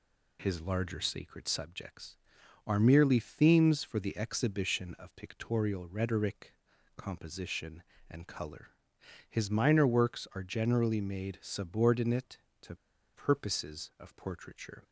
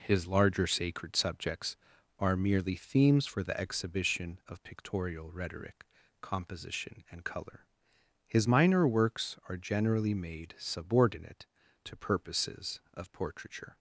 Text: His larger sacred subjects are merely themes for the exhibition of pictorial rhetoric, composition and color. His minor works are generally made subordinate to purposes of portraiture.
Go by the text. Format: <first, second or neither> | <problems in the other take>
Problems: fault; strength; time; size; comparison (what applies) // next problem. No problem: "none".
second | pauses between "to" and "purposes"; at 12.7 s; 0.39 s long